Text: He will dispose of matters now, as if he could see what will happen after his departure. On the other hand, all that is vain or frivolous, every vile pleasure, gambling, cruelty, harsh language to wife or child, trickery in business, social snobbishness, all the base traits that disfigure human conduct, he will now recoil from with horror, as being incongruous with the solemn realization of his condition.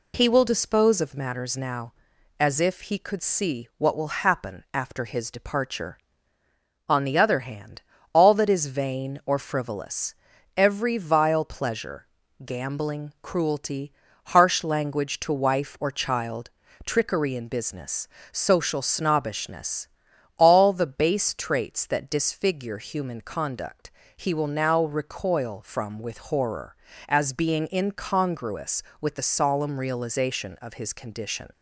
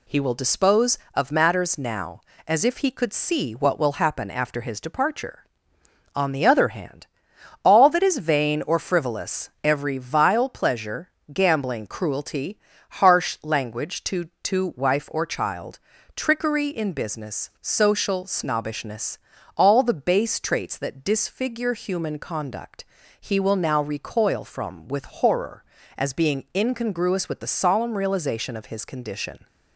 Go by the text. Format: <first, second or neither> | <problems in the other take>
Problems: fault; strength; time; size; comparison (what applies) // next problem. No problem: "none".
first | says "to" twice; at 14.4 s